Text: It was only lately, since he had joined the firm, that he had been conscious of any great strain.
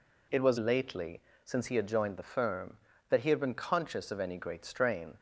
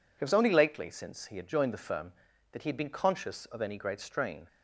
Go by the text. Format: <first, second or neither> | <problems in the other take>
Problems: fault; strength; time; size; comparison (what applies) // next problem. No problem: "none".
second | skips "only"; at 0.5 s